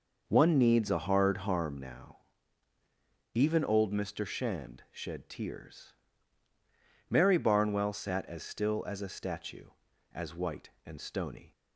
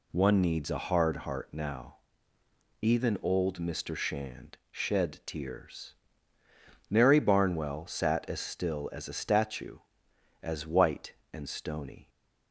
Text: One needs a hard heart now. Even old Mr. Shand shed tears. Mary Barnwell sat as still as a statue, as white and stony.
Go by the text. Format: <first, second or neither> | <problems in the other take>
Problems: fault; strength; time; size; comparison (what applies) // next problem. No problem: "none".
second | says "harm" for "heart"; at 1.3 s